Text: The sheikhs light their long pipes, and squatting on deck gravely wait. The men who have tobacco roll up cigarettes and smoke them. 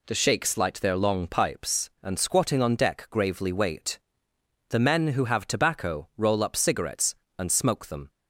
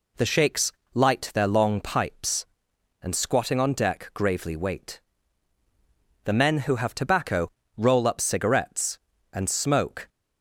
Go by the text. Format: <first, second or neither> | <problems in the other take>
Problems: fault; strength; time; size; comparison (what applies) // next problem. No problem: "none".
first | pauses between "sheikhs" and "light"; slight; at 0.7 s; 0.20 s long // pauses between "tobacco" and "roll"; slight; at 7.4 s; 0.28 s long // stops before "them"; at 10.0 s